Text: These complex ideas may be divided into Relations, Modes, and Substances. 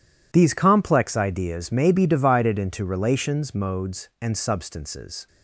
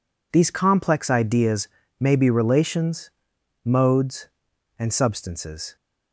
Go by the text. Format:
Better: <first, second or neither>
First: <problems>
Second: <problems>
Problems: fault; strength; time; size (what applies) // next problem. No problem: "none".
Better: first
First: none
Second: pauses between "ideas" and "may"; slight; at 1.6 s; 0.32 s long // skips "divided into"; at 2.2 s